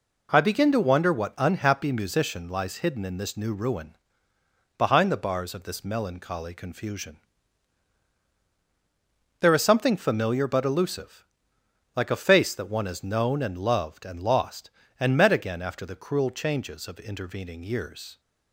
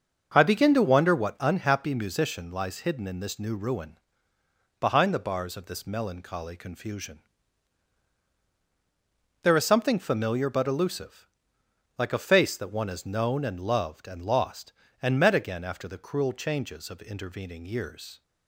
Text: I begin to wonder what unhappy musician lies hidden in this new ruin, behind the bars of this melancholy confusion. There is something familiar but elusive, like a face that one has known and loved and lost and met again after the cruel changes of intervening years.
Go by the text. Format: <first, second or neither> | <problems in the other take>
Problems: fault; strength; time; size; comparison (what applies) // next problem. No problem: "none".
first | starts louder than the rest; until 1.5 s; 6.5 dB